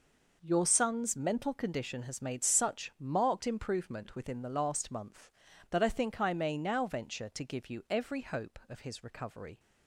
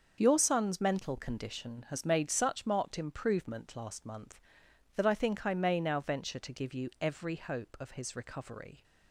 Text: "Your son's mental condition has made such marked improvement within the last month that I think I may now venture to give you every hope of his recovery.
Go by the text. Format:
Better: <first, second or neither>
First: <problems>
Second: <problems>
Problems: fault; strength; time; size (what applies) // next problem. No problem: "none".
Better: first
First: none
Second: starts louder than the rest; until 1.2 s; 6.5 dB // skips "within the"; at 3.7 s